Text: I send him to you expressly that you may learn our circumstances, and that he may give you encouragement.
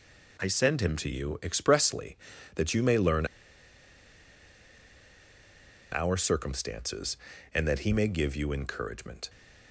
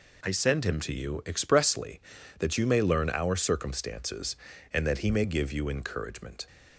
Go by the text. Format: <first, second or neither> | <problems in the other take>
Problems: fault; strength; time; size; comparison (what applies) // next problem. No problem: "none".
second | pauses between "learn" and "our"; strong; at 3.2 s; 2.6 s long